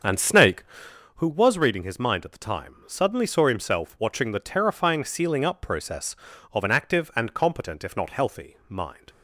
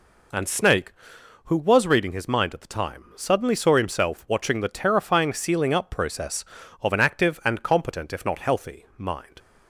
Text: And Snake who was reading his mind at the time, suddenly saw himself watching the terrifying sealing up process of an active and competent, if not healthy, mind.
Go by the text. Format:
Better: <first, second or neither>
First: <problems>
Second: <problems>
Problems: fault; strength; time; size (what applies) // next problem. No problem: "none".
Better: second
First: starts louder than the rest; until 1.0 s; 7 dB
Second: none